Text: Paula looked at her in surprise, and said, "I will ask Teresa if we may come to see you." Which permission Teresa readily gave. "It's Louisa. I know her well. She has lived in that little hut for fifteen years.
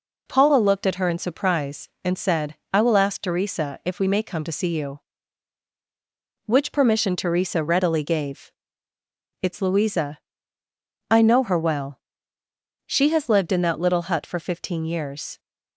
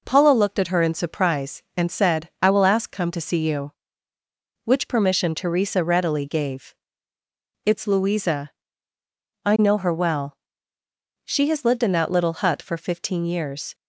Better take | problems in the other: first | skips "Teresa if we may"; at 2.9 s

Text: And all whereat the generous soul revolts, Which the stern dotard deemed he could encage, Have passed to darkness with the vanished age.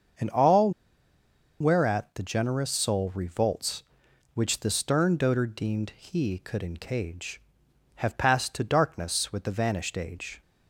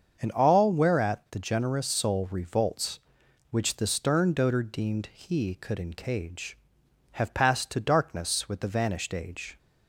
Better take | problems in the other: second | starts louder than the rest; until 2.1 s; 6.5 dB; also in the second // pauses between "all" and "whereat"; noticeable; at 0.7 s; 0.90 s long

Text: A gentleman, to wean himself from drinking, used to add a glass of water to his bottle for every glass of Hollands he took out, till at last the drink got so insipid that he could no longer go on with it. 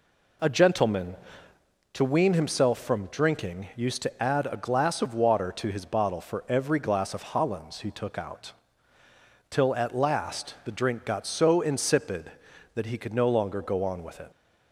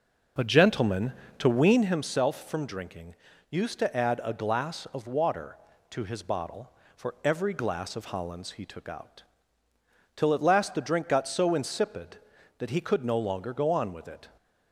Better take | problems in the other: first | starts louder than the rest; noticeable; until 2.0 s; 5 dB

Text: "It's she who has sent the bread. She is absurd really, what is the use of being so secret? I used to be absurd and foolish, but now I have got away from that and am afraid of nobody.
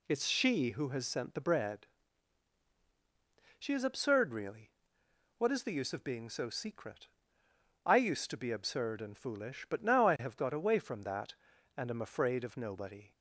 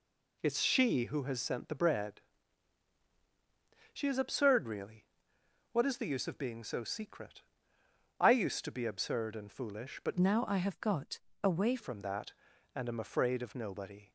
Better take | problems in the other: first | changes voice from "now" to "away"; from 10.1 to 11.7 s; 1.6 s long // pauses between "got" and "away"; slight; at 11.2 s; 0.22 s long

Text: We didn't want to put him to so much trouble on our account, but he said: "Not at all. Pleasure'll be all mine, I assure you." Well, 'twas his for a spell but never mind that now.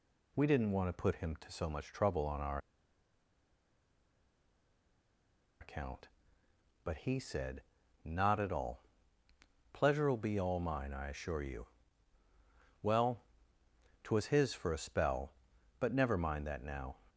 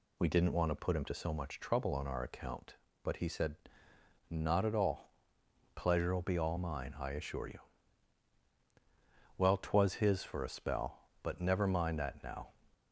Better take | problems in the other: second | pauses between "our" and "account"; strong; at 2.5 s; 3.0 s long

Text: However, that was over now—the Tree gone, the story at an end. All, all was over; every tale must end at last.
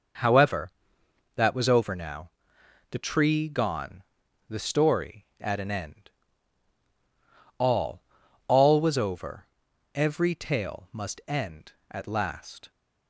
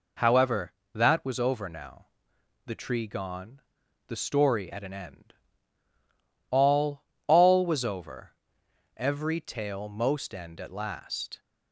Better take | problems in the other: first | says "most" for "must"; at 9.8 s

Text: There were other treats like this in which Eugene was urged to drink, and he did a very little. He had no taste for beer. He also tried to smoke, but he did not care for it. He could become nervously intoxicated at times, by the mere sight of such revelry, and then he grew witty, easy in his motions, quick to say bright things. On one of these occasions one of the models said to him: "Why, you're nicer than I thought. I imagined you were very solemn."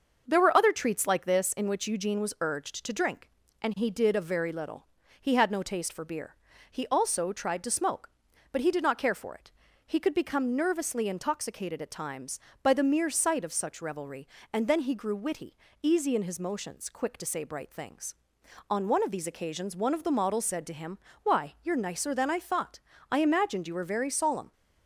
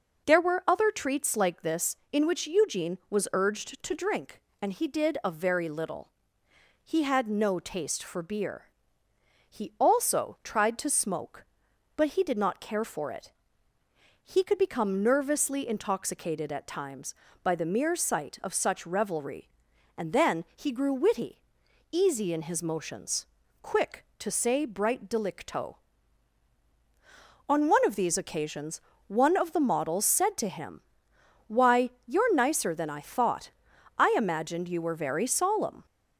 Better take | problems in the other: first | says "delicto" for "things"; at 25.0 s // pauses between "occasions" and "one"; slight; at 28.8 s; 0.26 s long

